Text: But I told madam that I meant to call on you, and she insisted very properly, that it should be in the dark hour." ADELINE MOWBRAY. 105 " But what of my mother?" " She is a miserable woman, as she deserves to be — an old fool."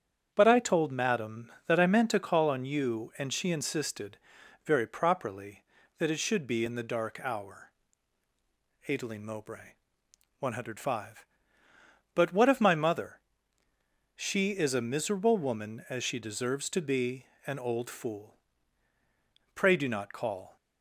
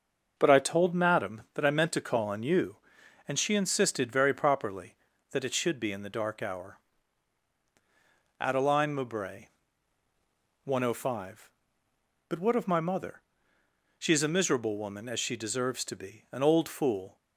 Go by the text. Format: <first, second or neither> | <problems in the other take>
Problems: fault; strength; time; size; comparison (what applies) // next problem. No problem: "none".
second | starts louder than the rest; strong; until 1.3 s; 8 dB; also in the second // pauses between "insisted" and "very"; noticeable; at 4.1 s; 0.48 s long // goes on to say "Pray do not call"; noticeable; from 19.5 s on; 1.0 s long